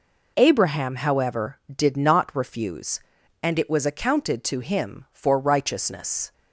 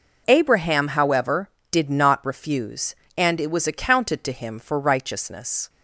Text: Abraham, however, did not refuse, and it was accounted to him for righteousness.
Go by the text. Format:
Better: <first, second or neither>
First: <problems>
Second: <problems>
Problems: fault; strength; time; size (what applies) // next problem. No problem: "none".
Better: neither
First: none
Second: none